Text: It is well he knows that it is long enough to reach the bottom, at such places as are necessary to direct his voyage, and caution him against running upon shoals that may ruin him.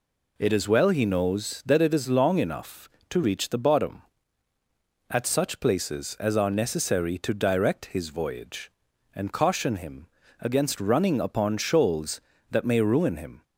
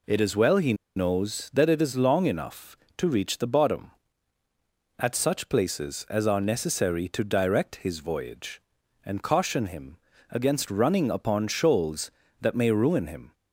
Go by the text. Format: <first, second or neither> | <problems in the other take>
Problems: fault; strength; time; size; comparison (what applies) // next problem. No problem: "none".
first | pauses between "he" and "knows"; slight; at 0.7 s; 0.22 s long // pauses between "him" and "against"; slight; at 9.9 s; 0.32 s long; slight in the first